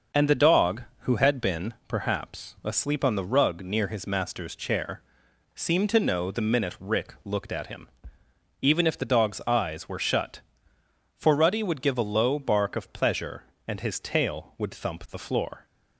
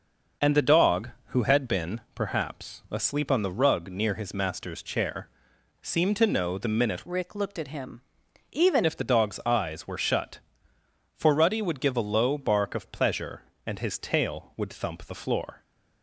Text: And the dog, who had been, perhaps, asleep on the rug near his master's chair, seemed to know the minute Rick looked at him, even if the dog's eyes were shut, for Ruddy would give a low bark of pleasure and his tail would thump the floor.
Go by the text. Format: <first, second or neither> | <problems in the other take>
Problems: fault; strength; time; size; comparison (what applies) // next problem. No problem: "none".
first | starts louder than the rest; until 1.6 s; 6 dB; noticeable in the first // changes voice from "Rick" to "even"; from 7.0 to 8.8 s; 1.8 s long